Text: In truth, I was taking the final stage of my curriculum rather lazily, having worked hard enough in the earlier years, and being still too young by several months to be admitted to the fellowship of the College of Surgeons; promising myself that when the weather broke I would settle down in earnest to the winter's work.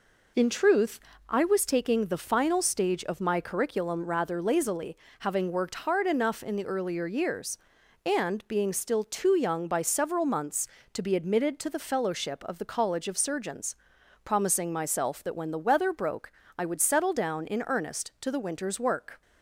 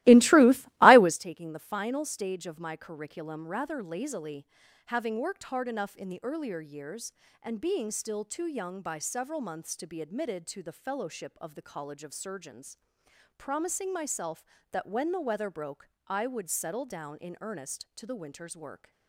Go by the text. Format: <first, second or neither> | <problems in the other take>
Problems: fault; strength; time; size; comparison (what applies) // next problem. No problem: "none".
first | starts louder than the rest; strong; until 1.2 s; 17.5 dB // pauses between "broke" and "I"; slight; at 15.8 s; 0.18 s long; slight in the first